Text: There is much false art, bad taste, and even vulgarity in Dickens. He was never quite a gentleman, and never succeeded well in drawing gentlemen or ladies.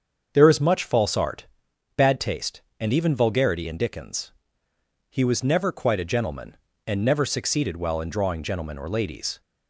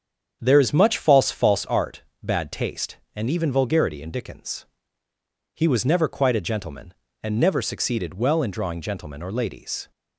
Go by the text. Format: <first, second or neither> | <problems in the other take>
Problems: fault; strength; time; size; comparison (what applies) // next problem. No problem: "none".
first | starts louder than the rest; strong; until 1.4 s; 8 dB; also in the first // says "false" twice; at 1.3 s